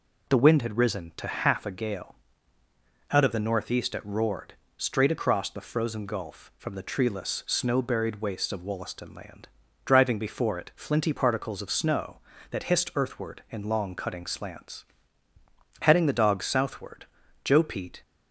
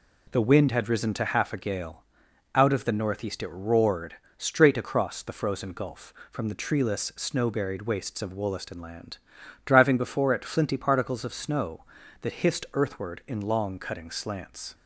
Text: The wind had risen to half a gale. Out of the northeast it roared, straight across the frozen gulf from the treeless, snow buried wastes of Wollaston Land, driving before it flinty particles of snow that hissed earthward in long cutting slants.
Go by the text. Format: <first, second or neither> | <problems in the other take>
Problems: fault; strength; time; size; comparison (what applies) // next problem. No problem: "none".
second | goes on to say "Heading the dogs southward Joe Pete"; strong; from 15.8 s on; 2.2 s long